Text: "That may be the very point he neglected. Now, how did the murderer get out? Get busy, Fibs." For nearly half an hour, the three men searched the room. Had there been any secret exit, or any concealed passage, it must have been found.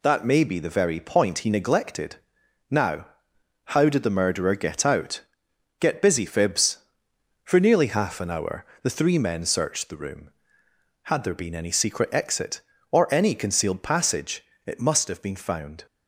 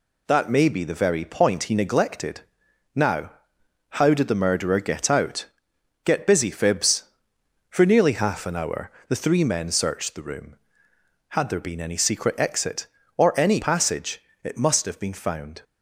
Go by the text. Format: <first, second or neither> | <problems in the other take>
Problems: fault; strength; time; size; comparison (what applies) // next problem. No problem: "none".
first | skips "concealed"; at 13.6 s